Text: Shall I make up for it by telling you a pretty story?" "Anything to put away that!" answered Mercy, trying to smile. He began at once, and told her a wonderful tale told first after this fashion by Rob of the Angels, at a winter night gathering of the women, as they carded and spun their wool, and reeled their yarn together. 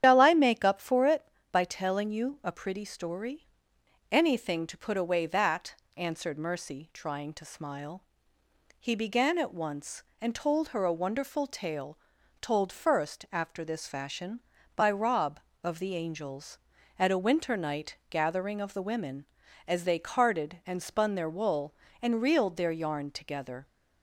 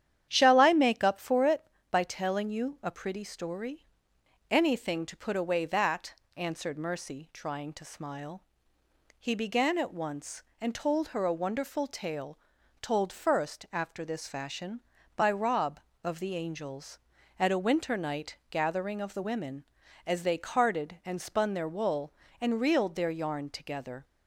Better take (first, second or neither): second